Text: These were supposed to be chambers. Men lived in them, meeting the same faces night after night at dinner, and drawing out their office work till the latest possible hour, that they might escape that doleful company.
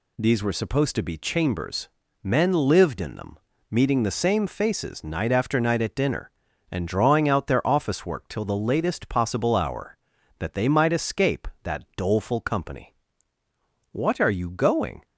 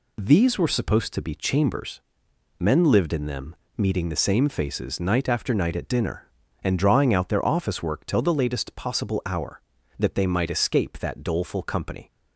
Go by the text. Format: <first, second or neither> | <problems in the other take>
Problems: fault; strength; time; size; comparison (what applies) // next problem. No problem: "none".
second | goes on to say "What are you going"; noticeable; from 13.9 s on; 1.1 s long